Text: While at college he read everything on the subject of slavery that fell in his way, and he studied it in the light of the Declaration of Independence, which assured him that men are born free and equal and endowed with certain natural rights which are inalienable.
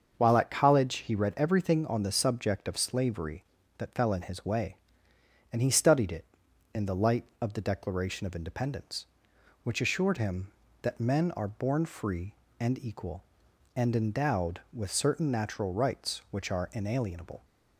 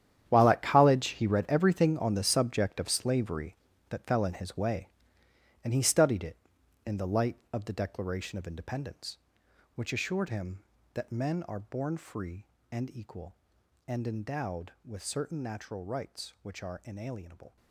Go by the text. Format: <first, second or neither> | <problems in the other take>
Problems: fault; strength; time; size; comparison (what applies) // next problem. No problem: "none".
first | gets quieter; strong; throughout; 15 dB // starts louder than the rest; strong; until 1.3 s; 10 dB; also in the first